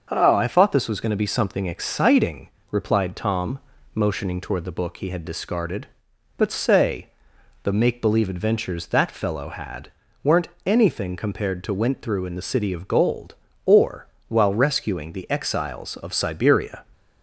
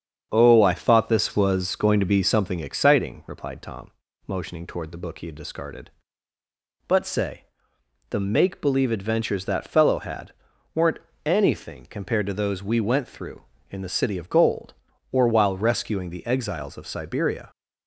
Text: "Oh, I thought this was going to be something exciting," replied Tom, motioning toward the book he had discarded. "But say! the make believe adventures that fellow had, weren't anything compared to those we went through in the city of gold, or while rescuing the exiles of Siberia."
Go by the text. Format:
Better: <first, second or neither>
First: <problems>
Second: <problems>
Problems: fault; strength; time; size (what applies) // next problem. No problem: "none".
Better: second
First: starts louder than the rest; until 1.1 s; 6.5 dB // pauses between "weren't" and "anything"; slight; at 10.4 s; 0.16 s long // skips "those we"; at 11.7 s // pauses between "or" and "while"; slight; at 14.0 s; 0.22 s long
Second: starts louder than the rest; strong; until 1.3 s; 8 dB // pauses between "weren't" and "anything"; slight; at 11.0 s; 0.26 s long